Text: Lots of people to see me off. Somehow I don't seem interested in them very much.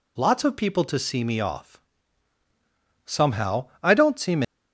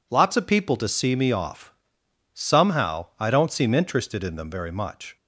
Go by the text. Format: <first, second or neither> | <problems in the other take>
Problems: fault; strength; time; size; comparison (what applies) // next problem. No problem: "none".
second | stops before "interested in them very much"; at 4.4 s